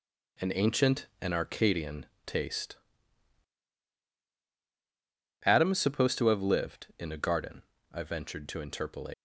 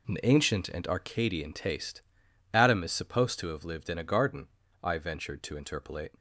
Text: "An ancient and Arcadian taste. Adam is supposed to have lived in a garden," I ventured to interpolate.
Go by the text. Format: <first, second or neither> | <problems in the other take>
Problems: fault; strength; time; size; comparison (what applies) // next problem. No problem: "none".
second | pauses between "Arcadian" and "taste"; slight; at 2.0 s; 0.22 s long // leaves "interpolate" unfinished; at 9.1 s; 85 ms